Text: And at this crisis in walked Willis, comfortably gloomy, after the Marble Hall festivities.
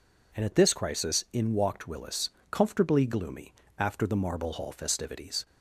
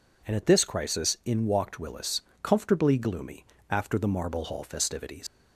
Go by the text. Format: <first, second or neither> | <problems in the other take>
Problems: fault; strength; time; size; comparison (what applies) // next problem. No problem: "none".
first | leaves "festivities" unfinished; at 5.2 s; 100 ms